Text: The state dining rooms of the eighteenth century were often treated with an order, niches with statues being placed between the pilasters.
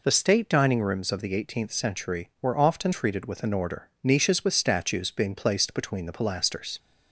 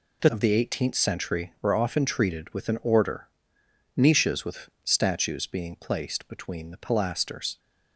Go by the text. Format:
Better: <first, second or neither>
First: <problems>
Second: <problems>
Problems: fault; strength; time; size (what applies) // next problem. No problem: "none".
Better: first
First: none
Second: skips "state dining rooms"; at 0.2 s // pauses between "with" and "statues"; slight; at 4.6 s; 0.16 s long